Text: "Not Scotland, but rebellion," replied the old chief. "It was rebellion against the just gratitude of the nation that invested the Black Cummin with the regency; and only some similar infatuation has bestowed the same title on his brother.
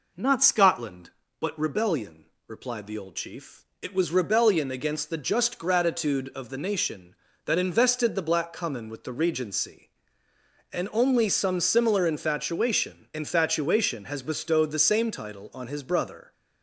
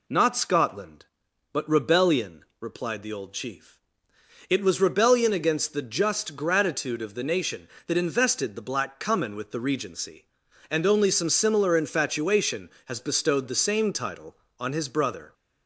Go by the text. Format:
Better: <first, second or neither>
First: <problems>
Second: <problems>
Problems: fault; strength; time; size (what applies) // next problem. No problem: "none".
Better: second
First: says "infatuation" twice; at 13.1 s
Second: none